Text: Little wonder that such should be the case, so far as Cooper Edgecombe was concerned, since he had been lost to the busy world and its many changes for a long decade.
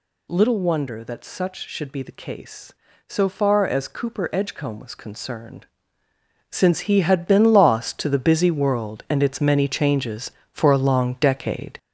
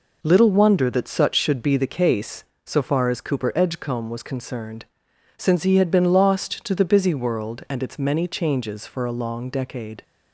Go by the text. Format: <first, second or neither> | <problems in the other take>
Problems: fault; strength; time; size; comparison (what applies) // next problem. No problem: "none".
second | gets louder; throughout; 6.5 dB